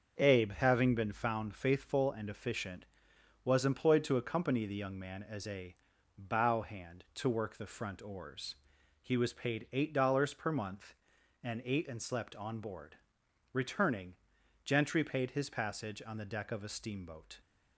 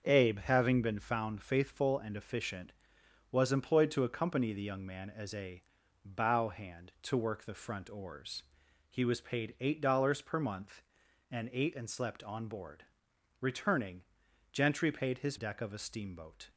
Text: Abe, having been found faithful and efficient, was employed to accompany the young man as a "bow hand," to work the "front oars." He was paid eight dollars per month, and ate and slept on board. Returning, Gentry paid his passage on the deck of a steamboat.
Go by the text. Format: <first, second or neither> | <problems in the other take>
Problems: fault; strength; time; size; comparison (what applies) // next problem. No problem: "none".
first | starts louder than the rest; until 1.0 s; 6.5 dB; also in the first // pauses between "a" and "bow"; at 5.6 s; 0.40 s long; also in the first // skips "passage on the"; at 15.3 s